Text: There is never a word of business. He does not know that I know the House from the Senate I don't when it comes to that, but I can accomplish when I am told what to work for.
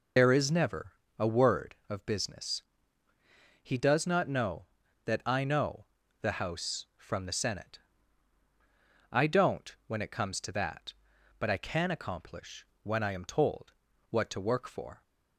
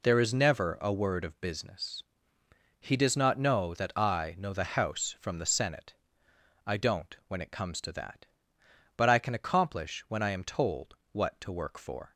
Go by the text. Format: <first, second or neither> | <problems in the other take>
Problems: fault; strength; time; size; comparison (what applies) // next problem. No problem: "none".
second | loses the start of "There"; at 0.1 s; 65 ms // pauses between "never" and "a"; slight; at 0.9 s; 0.28 s long // pauses between "know" and "the"; at 5.8 s; 0.38 s long // pauses between "Senate" and "I"; strong; at 7.7 s; 1.3 s long; noticeable in the second // pauses between "accomplish" and "when"; slight; at 12.6 s; 0.18 s long // pauses between "told" and "what"; at 13.7 s; 0.38 s long; slight in the second